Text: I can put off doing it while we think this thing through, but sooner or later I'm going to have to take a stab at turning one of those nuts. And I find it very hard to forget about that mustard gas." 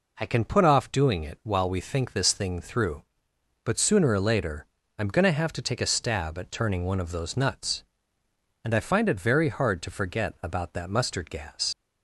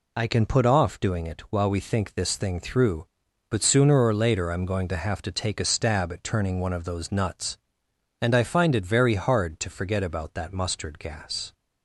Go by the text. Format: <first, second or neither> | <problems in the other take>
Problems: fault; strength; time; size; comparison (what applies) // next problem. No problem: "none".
second | pauses between "later" and "I'm"; slight; at 4.6 s; 0.30 s long // leaves "gas" unfinished; at 11.7 s; 105 ms